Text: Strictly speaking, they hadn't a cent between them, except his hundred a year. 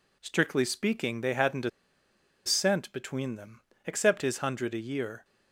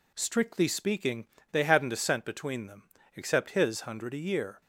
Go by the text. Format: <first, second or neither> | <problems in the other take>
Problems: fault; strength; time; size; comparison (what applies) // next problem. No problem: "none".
second | pauses between "a" and "cent"; noticeable; at 1.6 s; 0.76 s long